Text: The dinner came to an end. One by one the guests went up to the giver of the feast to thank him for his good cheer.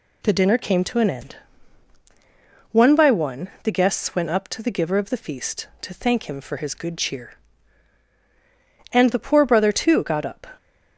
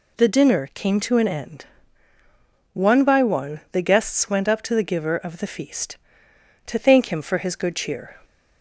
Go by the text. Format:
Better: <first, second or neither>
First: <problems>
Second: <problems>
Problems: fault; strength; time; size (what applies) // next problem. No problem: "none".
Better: second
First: goes on to say "And the poor brother too got up"; from 8.9 s on; 1.5 s long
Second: none